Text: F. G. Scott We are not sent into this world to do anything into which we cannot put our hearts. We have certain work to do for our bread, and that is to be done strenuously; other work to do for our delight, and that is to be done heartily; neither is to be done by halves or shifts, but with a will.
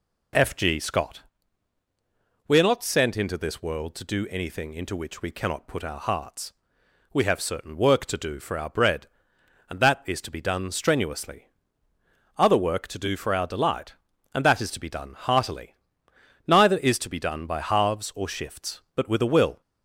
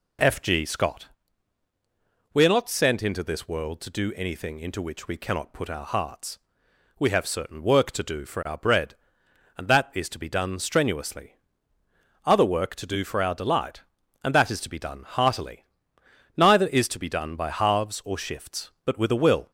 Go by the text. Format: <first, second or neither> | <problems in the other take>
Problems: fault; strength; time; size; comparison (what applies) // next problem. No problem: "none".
neither | pauses between "Scott" and "We"; strong; the same in both